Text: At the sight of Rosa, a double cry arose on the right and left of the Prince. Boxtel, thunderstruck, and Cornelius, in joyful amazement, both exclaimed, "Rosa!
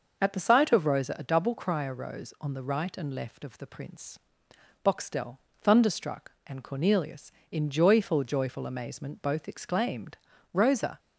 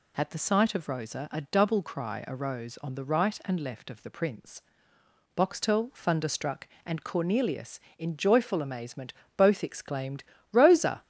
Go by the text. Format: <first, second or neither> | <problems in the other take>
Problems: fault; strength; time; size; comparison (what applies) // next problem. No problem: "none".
second | says "joyful" twice; at 8.2 s